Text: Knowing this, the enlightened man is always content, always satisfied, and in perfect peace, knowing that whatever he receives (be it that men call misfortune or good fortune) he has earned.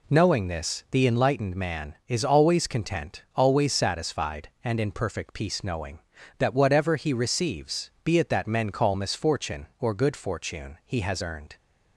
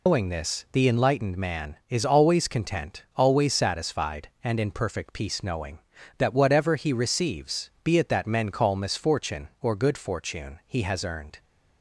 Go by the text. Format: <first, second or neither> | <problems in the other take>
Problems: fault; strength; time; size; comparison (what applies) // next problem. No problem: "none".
first | loses the start of "Knowing"; at 0.0 s; 185 ms